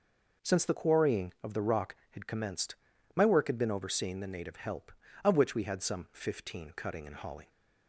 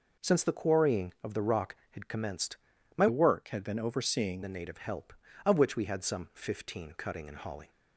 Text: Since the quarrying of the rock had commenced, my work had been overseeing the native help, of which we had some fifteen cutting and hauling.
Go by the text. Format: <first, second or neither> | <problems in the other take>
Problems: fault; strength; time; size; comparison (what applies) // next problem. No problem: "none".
first | changes voice from "work" to "overseeing"; from 3.0 to 4.4 s; 1.4 s long